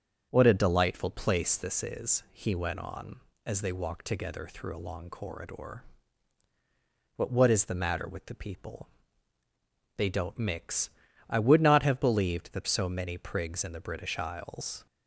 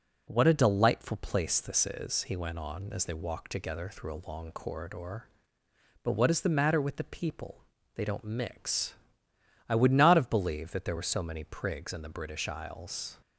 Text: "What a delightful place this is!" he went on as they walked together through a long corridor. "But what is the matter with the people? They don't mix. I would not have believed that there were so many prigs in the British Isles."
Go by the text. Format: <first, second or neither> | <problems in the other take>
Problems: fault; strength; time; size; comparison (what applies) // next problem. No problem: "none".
second | starts louder than the rest; strong; until 1.3 s; 7.5 dB // skips "there were"; at 12.6 s